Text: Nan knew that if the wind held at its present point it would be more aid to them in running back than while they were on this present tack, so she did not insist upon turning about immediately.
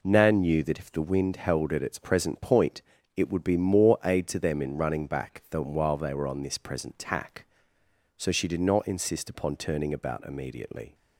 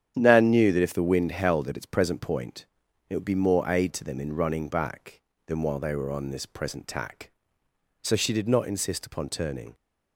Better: first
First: pauses between "point" and "it"; slight; at 2.8 s; 0.34 s long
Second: starts louder than the rest; strong; until 1.1 s; 9 dB // pauses between "point" and "it"; at 2.6 s; 0.44 s long // stops before "about immediately"; at 9.7 s

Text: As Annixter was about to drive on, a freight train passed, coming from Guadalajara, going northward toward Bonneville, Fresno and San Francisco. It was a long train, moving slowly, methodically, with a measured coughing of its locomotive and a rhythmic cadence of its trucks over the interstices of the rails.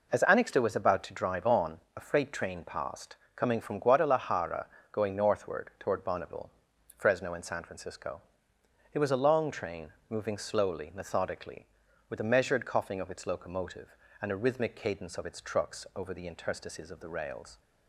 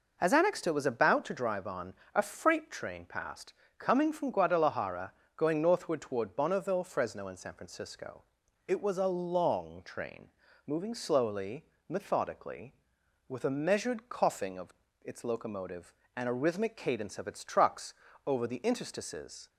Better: first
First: none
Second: pauses between "of" and "its"; slight; at 14.7 s; 0.30 s long // pauses between "trucks" and "over"; slight; at 17.9 s; 0.32 s long // stops before "of the rails"; at 19.4 s

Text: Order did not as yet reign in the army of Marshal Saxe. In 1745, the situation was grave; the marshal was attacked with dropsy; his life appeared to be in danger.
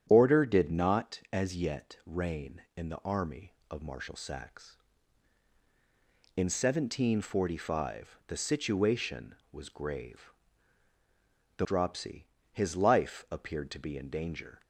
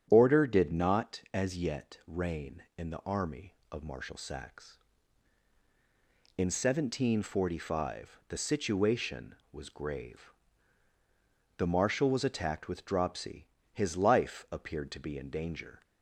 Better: second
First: starts louder than the rest; strong; until 1.1 s; 9 dB // skips "marshal was attacked with"; at 11.6 s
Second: starts louder than the rest; strong; until 1.1 s; 9 dB

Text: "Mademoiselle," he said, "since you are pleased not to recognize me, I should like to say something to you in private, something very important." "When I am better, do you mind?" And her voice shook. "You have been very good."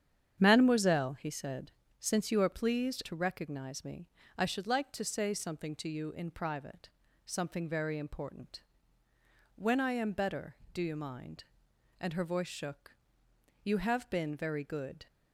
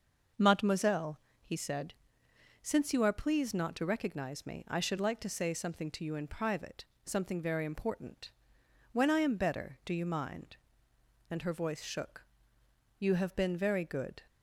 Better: second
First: starts louder than the rest; strong; until 1.4 s; 9 dB // skips "not"; at 3.0 s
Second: starts louder than the rest; noticeable; until 1.6 s; 6 dB

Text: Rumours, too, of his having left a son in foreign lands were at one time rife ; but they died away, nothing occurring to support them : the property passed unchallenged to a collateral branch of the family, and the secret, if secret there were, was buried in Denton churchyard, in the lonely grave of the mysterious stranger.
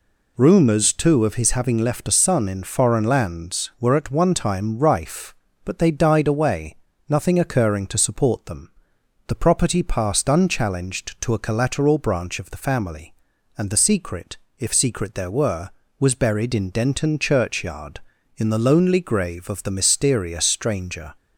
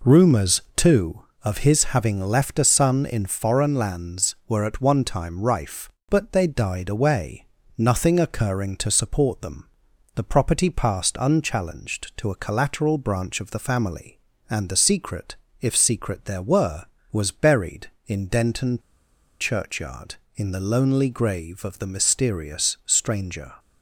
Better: first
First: none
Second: pauses between "Denton" and "churchyard"; noticeable; at 18.8 s; 0.60 s long

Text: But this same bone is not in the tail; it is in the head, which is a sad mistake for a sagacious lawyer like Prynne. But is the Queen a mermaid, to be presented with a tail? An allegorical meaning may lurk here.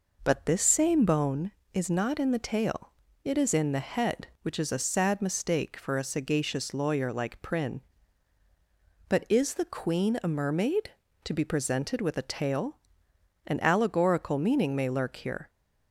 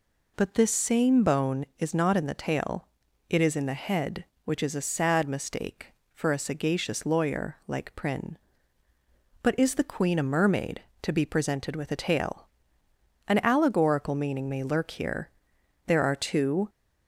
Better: first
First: none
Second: goes on to say "There are two"; noticeable; from 15.8 s on; 0.82 s long

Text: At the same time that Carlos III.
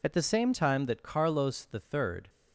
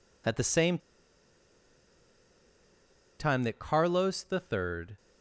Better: first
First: none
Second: pauses between "same" and "time"; strong; at 0.7 s; 2.4 s long

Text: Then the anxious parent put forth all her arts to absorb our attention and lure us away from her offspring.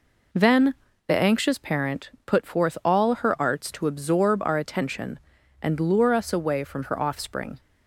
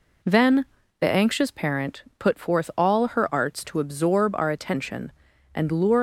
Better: first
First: pauses between "Then" and "the"; slight; at 0.7 s; 0.34 s long // pauses between "parent" and "put"; slight; at 2.0 s; 0.16 s long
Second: pauses between "Then" and "the"; slight; at 0.6 s; 0.36 s long // pauses between "parent" and "put"; slight; at 2.0 s; 0.16 s long // stops before "us away from her offspring"; at 5.9 s

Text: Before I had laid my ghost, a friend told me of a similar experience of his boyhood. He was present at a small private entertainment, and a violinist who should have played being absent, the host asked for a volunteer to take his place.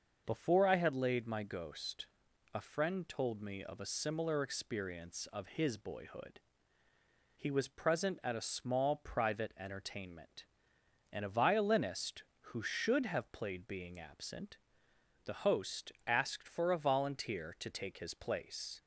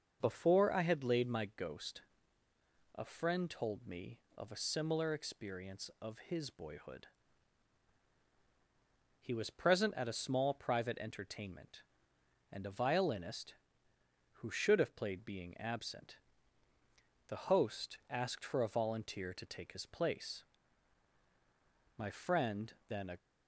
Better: first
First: starts louder than the rest; noticeable; until 1.2 s; 6 dB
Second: starts louder than the rest; noticeable; until 1.2 s; 6 dB // goes on to say "My friend then a"; noticeable; from 21.9 s on; 1.2 s long

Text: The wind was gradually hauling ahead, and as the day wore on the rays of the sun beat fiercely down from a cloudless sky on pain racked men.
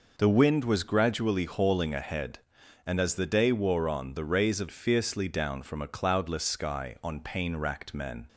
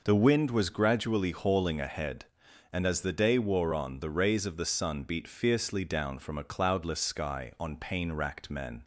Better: second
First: skips "the sun beat"; at 4.6 s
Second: none

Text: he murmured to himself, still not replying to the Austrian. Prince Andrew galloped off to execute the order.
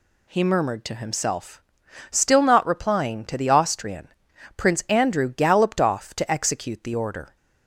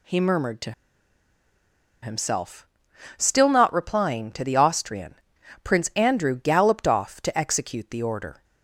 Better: first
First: none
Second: pauses between "to" and "himself"; strong; at 0.7 s; 1.3 s long

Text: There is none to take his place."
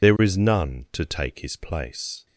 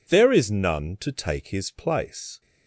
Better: second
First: loses the start of "There"; at 0.0 s; 30 ms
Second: none

